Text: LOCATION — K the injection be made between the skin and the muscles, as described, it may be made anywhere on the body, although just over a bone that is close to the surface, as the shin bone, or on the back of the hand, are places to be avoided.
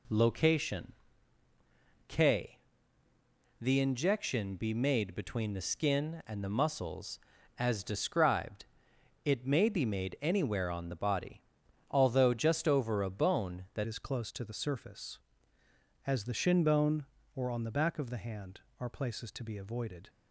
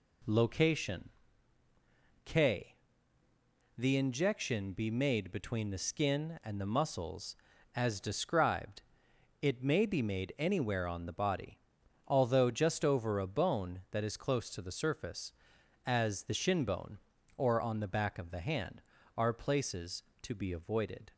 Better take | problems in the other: second | pauses between "K" and "the"; at 2.5 s; 1.0 s long; also in the second // changes voice at "is"; from 13.8 s on; 6.2 s long

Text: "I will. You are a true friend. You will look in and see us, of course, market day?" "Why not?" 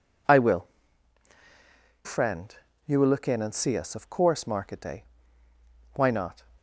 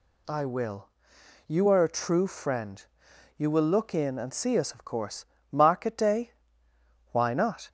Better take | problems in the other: second | skips "You are a true"; at 1.3 s

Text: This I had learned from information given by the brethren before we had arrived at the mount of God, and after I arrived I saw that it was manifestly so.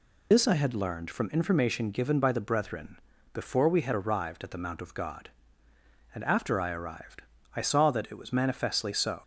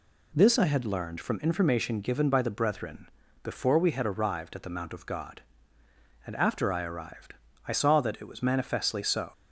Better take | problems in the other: second | loses the start of "This"; at 0.3 s; 85 ms // pauses between "brethren" and "before"; slight; at 3.0 s; 0.32 s long; slight in the second // pauses between "arrived" and "I"; slight; at 7.2 s; 0.34 s long; slight in the second

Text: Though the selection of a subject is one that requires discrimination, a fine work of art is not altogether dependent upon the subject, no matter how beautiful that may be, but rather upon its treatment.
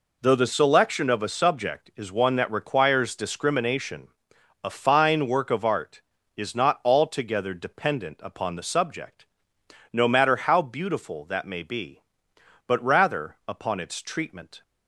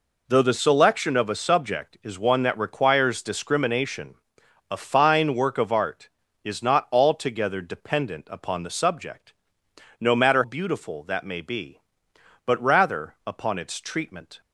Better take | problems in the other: first | skips "how"; at 10.4 s

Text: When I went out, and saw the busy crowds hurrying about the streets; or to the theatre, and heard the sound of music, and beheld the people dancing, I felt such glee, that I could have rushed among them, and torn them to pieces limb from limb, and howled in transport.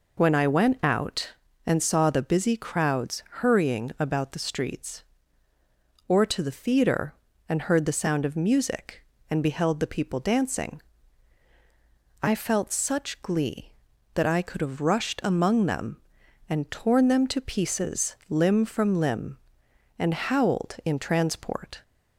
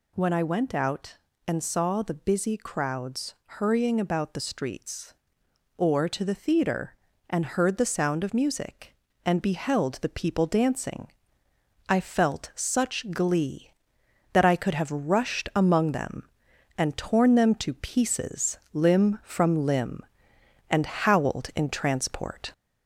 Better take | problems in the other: first | gets louder; slight; throughout; 2.5 dB

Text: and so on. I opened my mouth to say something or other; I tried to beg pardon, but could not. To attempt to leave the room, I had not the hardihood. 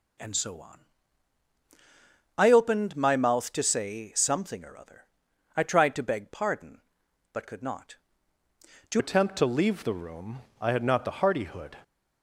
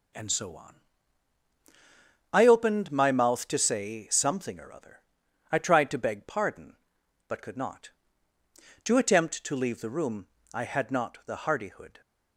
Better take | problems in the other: second | changes voice at "attempt"; from 8.9 s on; 2.8 s long

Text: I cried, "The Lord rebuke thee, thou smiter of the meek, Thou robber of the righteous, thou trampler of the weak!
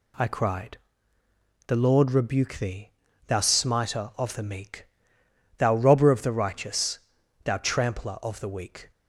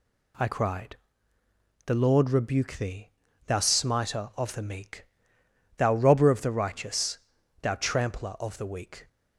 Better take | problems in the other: neither | none

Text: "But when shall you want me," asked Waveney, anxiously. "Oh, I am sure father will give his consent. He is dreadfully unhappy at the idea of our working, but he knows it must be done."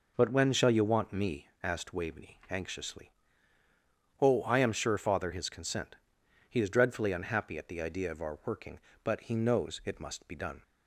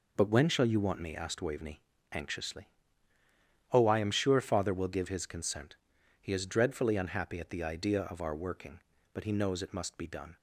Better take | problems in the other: second | skips "will give"; at 5.3 s

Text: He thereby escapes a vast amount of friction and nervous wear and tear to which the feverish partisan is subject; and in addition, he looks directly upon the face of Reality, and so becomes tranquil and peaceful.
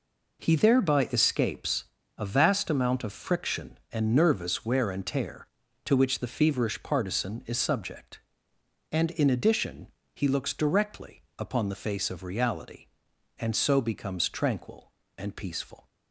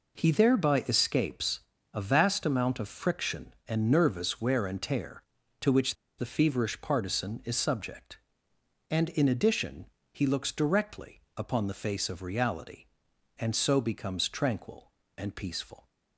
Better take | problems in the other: first | pauses between "escapes" and "a"; slight; at 1.6 s; 0.32 s long; slight in the first // pauses between "which" and "the"; slight; at 5.9 s; 0.23 s long // pauses between "directly" and "upon"; slight; at 11.1 s; 0.16 s long; slight in the first

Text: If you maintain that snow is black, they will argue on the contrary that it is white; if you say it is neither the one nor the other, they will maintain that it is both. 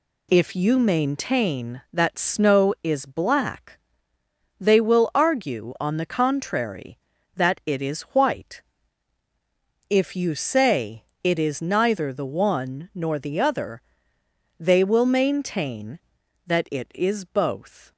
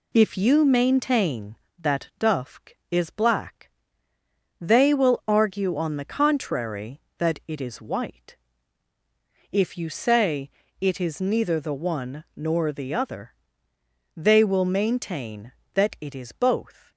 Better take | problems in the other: first | says "dufk" for "snow"; at 2.1 s // pauses between "say" and "it"; slight; at 10.5 s; 0.28 s long; slight in the first

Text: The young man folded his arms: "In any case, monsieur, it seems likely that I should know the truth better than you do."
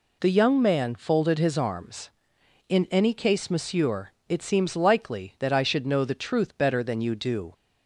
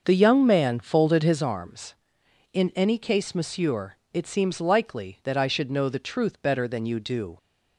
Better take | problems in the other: first | starts louder than the rest; until 1.4 s; 6.5 dB

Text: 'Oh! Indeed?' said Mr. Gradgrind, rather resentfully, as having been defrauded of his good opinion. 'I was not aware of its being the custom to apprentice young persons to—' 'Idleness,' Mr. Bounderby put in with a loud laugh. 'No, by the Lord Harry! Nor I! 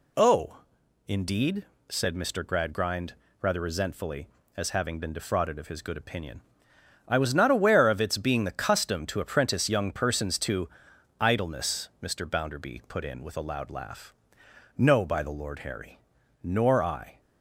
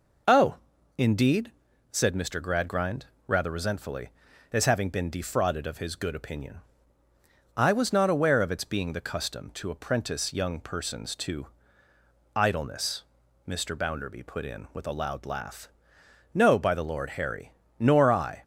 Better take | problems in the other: neither | none

